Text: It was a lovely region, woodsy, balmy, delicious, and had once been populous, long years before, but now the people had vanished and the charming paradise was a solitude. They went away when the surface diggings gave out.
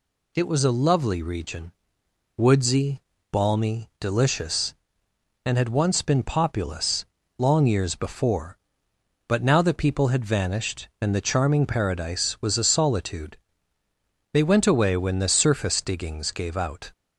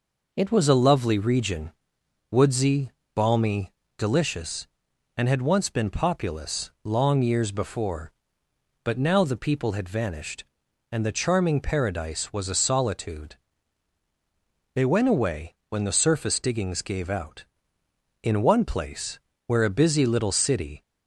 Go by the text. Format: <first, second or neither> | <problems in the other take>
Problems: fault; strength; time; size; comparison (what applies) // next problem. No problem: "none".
first | goes on to say "In one place where a busy little city"; strong; from 18.2 s on; 2.6 s long